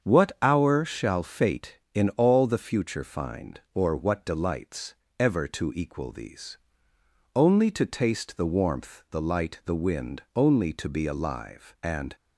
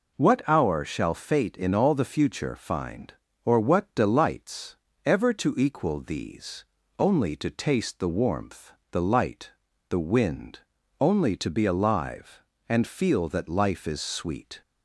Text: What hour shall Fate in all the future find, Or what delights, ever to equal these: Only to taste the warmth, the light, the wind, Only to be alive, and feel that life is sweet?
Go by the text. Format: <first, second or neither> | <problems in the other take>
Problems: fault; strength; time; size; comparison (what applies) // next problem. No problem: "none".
second | starts louder than the rest; strong; until 1.1 s; 7 dB // stops before "feel that life is sweet"; at 12.1 s